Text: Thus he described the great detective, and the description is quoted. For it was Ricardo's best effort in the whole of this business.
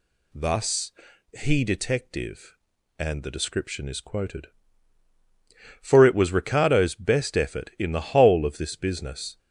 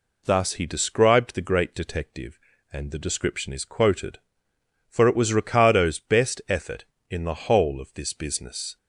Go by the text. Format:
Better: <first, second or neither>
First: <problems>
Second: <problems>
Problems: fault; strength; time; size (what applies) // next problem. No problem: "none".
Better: second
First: pauses between "Thus" and "he"; at 0.9 s; 0.44 s long // skips "described the great"; at 1.6 s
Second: none